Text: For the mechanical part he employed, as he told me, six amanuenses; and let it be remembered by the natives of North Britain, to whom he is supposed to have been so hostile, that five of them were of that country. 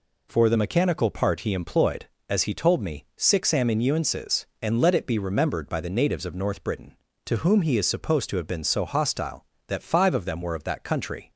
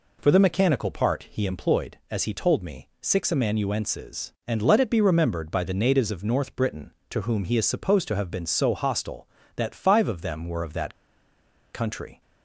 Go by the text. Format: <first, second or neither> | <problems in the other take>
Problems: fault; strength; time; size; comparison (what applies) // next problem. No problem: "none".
first | pauses between "that" and "country"; noticeable; at 10.9 s; 0.78 s long